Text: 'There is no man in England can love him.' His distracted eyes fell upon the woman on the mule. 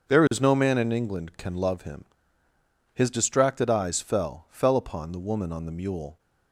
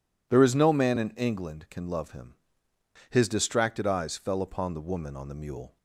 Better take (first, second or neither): second